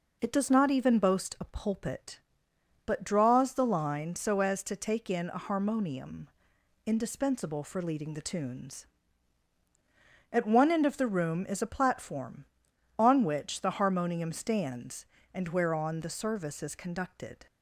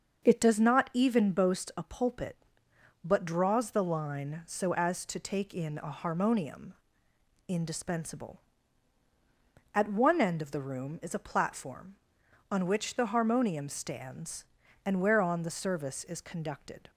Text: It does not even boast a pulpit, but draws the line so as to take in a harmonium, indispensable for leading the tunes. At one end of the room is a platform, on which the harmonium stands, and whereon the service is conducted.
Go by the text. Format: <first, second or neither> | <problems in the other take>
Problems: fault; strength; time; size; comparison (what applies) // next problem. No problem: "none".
first | starts louder than the rest; until 1.2 s; 6.5 dB // skips "for leading the tunes"; at 9.0 s